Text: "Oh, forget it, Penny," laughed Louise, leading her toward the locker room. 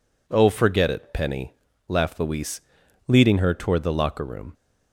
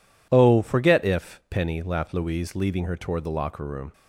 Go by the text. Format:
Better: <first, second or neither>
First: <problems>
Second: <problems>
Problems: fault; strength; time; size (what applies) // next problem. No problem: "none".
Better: first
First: none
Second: says "if" for "it"; at 1.0 s